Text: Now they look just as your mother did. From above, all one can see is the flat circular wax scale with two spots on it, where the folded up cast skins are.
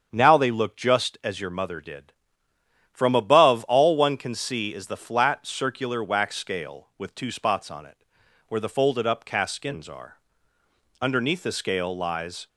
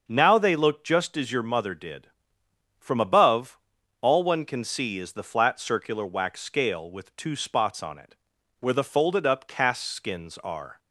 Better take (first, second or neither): second